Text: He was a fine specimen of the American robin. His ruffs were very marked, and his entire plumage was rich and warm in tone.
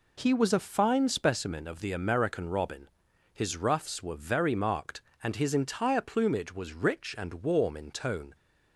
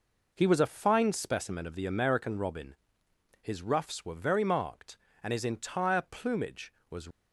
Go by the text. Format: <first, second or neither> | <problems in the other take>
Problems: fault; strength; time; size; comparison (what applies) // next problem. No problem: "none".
first | stops before "rich and warm in tone"; at 7.1 s